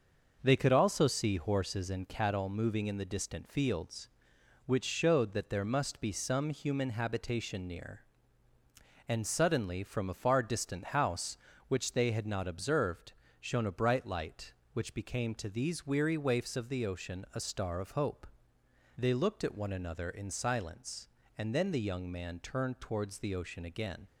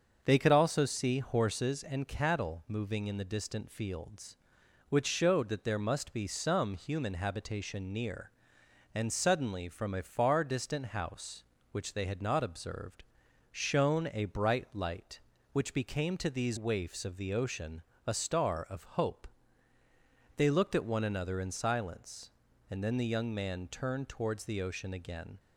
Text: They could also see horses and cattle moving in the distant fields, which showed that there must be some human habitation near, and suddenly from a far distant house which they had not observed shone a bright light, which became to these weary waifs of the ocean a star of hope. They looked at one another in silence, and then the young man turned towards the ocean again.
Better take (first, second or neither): first